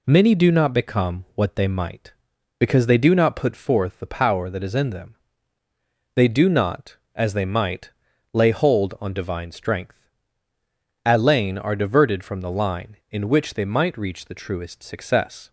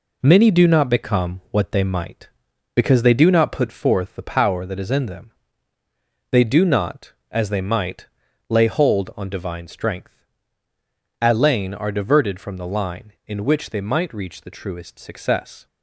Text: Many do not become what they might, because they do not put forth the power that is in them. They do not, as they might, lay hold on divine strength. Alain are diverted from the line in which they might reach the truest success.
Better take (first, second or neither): first